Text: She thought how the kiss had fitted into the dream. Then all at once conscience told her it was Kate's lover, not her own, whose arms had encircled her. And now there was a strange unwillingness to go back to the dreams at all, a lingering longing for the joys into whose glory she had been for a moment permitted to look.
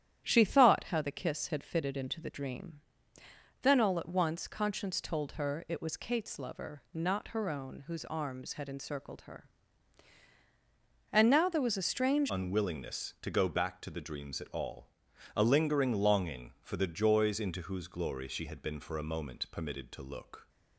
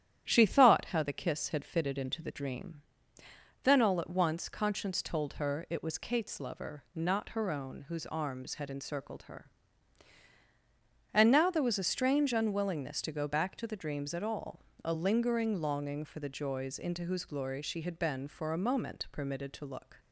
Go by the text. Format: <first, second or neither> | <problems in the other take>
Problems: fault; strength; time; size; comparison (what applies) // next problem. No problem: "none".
second | starts louder than the rest; strong; until 1.2 s; 10.5 dB; strong in the second // changes voice at "unwillingness"; from 12.3 s on; 8.1 s long